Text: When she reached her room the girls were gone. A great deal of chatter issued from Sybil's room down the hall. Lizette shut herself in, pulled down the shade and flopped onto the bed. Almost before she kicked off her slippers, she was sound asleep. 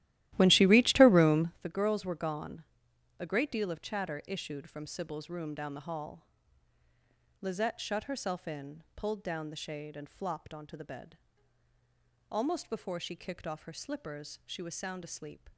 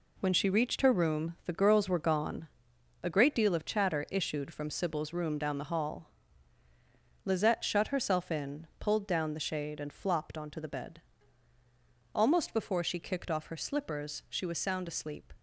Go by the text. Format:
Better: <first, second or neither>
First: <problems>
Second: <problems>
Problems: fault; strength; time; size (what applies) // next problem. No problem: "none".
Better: second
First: starts louder than the rest; strong; until 1.7 s; 15 dB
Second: none